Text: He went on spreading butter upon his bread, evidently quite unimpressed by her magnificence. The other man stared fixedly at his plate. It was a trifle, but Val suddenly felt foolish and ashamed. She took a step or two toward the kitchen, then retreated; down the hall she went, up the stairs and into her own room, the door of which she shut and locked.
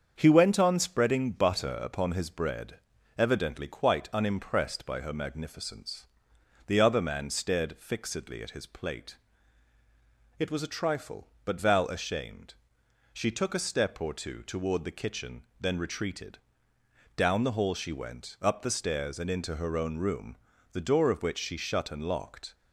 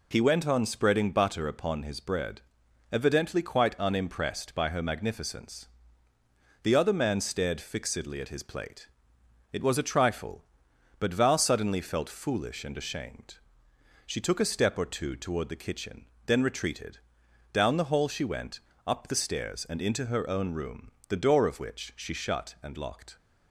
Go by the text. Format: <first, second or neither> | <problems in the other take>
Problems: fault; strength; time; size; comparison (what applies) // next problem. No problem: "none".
second | starts louder than the rest; until 1.1 s; 7 dB // skips "suddenly felt foolish and"; at 11.8 s